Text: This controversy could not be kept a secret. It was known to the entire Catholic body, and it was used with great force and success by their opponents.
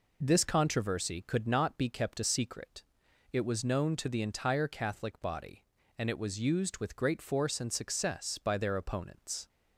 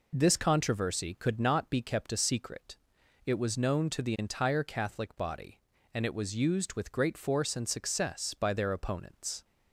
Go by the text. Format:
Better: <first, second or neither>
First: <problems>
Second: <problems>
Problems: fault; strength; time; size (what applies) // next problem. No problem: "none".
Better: neither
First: none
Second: none